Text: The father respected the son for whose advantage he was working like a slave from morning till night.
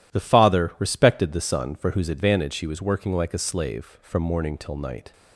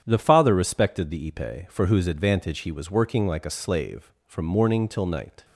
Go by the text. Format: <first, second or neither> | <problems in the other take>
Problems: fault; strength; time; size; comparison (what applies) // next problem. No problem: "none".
first | starts louder than the rest; strong; until 1.0 s; 9 dB // says "ipe" for "son"; at 1.3 s